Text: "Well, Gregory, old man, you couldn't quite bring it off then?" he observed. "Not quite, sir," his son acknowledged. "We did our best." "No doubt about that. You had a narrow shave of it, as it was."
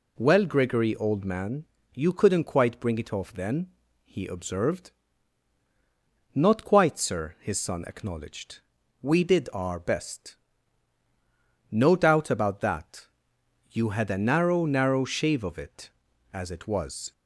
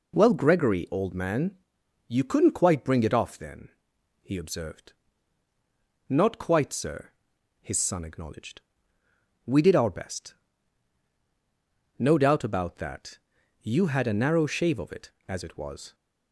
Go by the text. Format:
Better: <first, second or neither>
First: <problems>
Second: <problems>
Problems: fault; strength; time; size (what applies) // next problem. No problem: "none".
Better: second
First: says "narrow" twice; at 14.6 s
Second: none